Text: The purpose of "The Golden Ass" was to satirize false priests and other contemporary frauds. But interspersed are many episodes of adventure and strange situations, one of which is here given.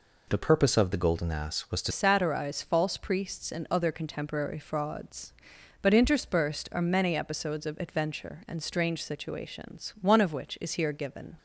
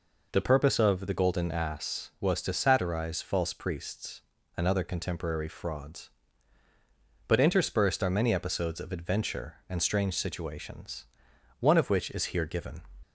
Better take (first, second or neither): second